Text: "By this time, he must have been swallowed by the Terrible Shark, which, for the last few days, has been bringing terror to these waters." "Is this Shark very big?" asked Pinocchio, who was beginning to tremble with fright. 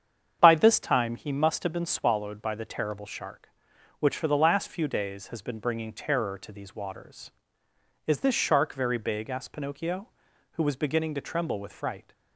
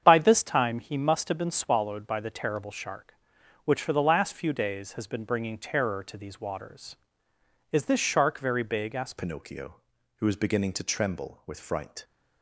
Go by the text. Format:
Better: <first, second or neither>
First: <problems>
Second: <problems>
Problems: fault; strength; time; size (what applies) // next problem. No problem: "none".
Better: first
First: starts louder than the rest; strong; until 1.4 s; 8 dB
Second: starts louder than the rest; strong; until 1.0 s; 8 dB // changes voice at "Pinocchio"; from 9.1 s on; 2.9 s long